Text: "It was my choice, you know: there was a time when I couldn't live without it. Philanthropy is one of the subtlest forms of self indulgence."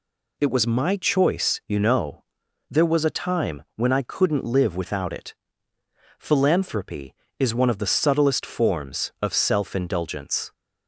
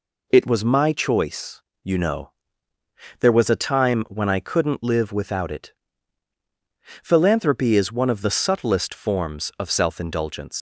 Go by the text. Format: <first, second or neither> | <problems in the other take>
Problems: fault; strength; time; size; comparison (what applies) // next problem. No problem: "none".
first | leaves "indulgence" unfinished; at 10.5 s; 90 ms